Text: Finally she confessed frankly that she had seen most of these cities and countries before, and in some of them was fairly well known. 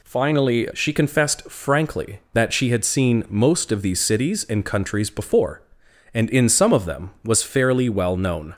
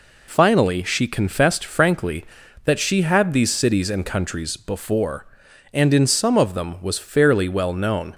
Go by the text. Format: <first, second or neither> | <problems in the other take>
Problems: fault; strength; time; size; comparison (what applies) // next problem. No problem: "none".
first | skips "seen most of"; at 3.3 s